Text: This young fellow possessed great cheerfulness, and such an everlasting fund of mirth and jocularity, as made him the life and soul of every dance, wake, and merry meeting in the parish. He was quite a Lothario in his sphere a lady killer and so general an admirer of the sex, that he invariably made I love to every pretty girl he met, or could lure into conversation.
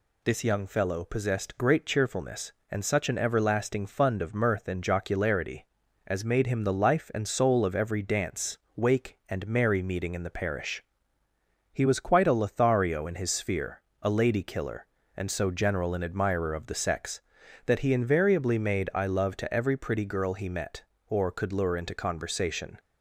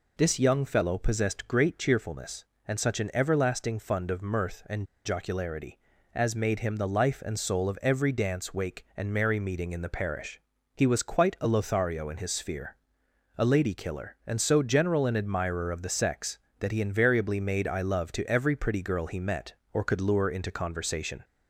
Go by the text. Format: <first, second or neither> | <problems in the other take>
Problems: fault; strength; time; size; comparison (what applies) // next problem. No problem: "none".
first | pauses between "and" and "jocularity"; slight; at 4.8 s; 0.20 s long // pauses between "sphere" and "a"; noticeable; at 12.7 s; 0.62 s long; slight in the first